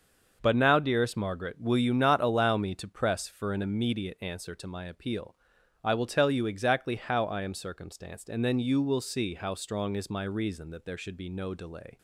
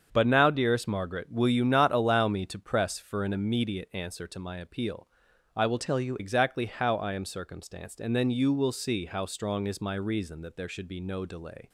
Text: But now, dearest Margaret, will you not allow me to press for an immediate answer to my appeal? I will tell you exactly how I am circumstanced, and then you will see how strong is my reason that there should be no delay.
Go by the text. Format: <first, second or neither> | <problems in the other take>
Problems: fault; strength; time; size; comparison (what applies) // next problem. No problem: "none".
first | starts louder than the rest; strong; until 1.1 s; 7 dB; also in the first // changes voice from "tell" to "you"; from 5.7 to 6.1 s; 0.4 s long